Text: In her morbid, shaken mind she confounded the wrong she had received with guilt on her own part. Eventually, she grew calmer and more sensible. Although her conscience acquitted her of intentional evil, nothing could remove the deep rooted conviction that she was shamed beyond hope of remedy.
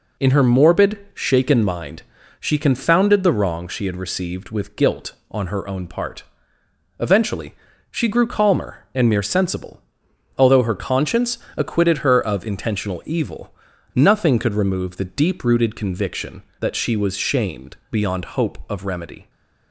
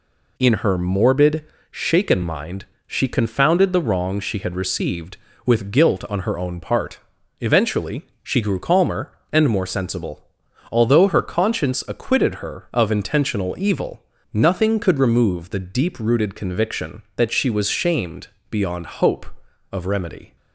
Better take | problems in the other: second | pauses between "mind" and "she"; at 2.0 s; 0.38 s long; slight in the second // says "mere" for "more"; at 9.0 s // pauses between "conscience" and "acquitted"; slight; at 11.3 s; 0.16 s long // pauses between "shamed" and "beyond"; slight; at 17.7 s; 0.16 s long; slight in the second

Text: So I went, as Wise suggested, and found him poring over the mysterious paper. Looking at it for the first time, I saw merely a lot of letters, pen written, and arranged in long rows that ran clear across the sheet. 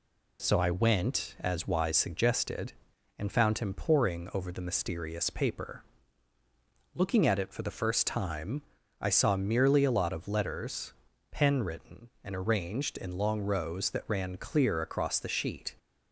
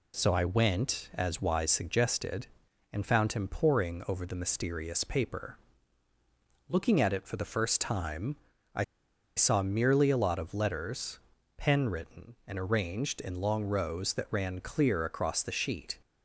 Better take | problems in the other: first | pauses between "I" and "saw"; noticeable; at 8.8 s; 0.52 s long

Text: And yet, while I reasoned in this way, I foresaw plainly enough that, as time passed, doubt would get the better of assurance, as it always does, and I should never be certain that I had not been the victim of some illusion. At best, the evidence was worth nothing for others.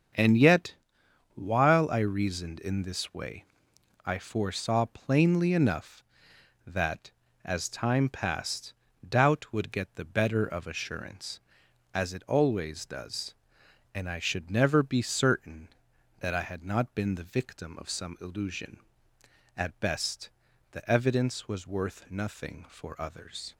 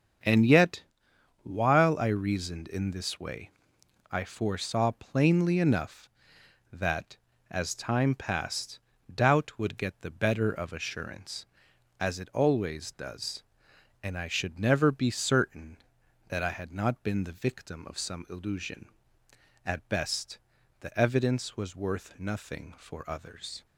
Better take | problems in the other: neither | starts louder than the rest; strong; the same in both

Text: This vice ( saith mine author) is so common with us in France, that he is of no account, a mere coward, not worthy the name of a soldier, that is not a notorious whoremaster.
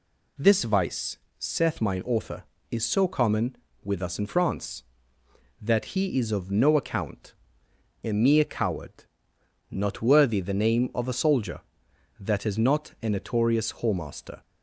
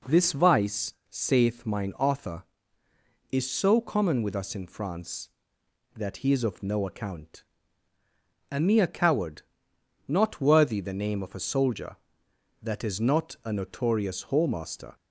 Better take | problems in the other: neither | none

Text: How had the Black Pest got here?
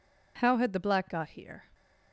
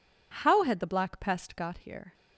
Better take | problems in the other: second | skips "Pest"; at 1.1 s

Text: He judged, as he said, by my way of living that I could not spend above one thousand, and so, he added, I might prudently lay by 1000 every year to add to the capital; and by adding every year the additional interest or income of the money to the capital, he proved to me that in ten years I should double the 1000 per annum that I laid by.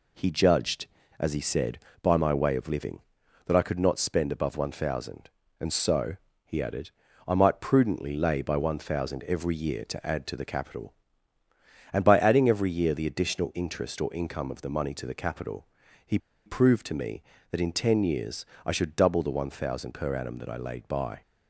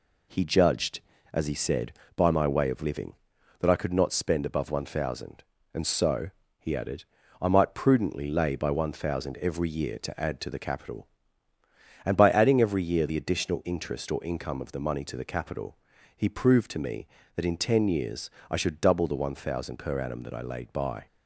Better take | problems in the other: second | pauses between "he" and "proved"; slight; at 16.1 s; 0.28 s long // pauses between "years" and "I"; slight; at 18.4 s; 0.22 s long; slight in the second

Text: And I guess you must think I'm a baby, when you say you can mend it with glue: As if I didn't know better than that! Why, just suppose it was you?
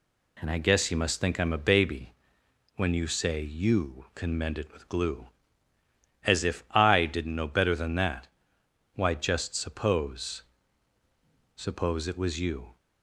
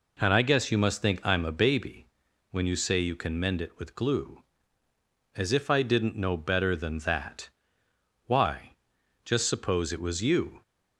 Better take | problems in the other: second | says "suppose" twice; at 11.5 s

